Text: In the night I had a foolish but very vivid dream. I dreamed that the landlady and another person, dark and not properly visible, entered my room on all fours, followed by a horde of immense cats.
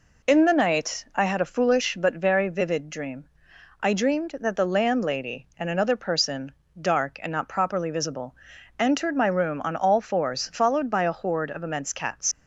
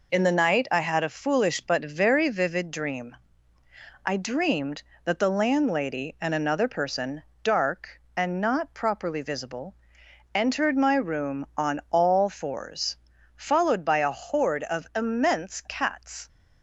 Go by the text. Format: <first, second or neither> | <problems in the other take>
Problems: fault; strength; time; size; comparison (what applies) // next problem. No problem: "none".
second | leaves "cats" unfinished; at 12.3 s; 65 ms